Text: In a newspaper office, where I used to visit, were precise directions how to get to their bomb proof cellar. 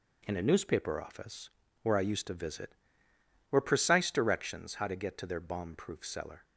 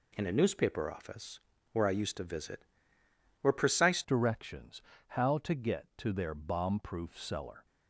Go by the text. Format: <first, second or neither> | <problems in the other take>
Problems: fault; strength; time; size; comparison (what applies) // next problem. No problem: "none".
first | changes voice at "directions"; from 4.0 s on; 3.6 s long // pauses between "directions" and "how"; slight; at 4.8 s; 0.24 s long